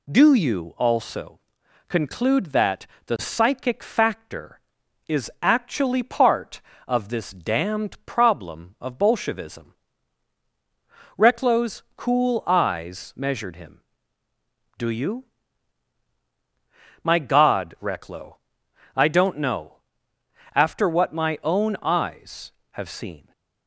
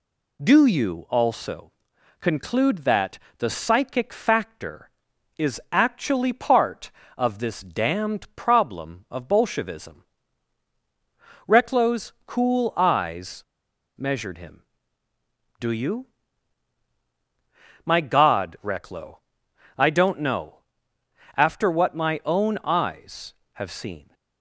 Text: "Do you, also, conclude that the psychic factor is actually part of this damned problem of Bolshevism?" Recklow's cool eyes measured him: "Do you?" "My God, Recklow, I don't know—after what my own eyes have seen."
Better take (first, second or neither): first